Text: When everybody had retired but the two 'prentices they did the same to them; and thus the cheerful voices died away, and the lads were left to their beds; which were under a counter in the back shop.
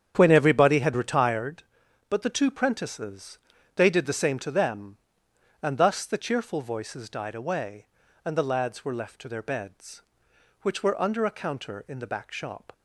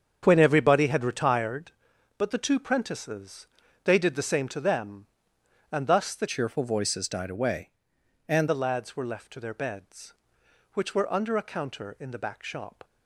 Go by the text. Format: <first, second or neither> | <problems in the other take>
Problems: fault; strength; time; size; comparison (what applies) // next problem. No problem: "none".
first | starts louder than the rest; strong; until 1.2 s; 7.5 dB; strong in the first // pauses between "prentices" and "they"; at 3.4 s; 0.38 s long; also in the first // changes voice from "cheerful" to "and"; from 6.2 to 8.4 s; 2.2 s long